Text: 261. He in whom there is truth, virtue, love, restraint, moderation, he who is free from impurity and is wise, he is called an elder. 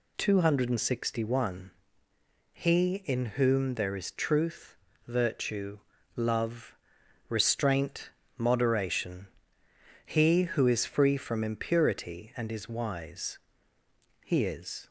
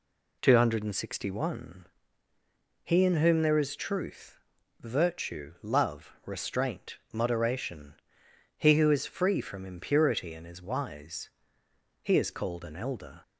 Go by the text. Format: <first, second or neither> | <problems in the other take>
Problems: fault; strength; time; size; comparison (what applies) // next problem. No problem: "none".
second | stops before "called an elder"; at 14.8 s